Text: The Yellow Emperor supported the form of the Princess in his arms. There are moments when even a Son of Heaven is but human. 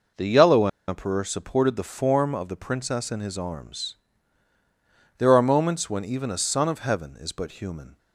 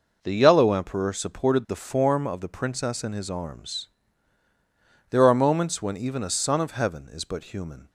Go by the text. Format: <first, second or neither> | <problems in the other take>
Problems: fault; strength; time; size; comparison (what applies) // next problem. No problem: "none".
second | pauses between "Yellow" and "Emperor"; slight; at 0.6 s; 0.20 s long